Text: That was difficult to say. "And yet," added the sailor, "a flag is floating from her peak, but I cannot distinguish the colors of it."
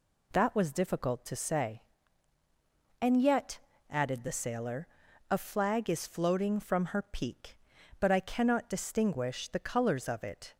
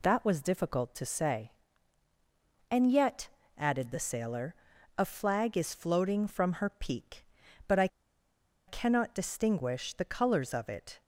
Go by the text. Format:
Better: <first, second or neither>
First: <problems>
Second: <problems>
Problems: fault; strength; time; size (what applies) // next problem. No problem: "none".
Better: first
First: none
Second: pauses between "I" and "cannot"; noticeable; at 7.8 s; 0.80 s long